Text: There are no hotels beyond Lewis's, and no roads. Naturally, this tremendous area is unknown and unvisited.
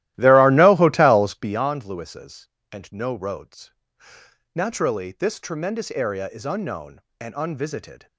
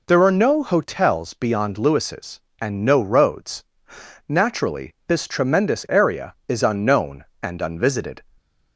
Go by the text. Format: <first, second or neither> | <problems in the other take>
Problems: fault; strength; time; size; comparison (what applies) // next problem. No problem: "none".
second | starts louder than the rest; strong; until 1.7 s; 15 dB